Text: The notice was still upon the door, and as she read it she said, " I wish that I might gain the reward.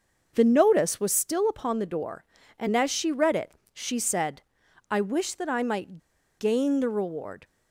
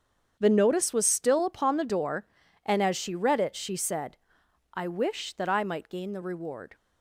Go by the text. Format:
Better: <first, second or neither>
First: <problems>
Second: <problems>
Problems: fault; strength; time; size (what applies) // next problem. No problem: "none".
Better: second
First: starts louder than the rest; until 1.3 s; 6.5 dB // pauses between "it" and "she"; slight; at 3.5 s; 0.20 s long // pauses between "might" and "gain"; at 6.0 s; 0.38 s long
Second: starts louder than the rest; strong; until 1.4 s; 7.5 dB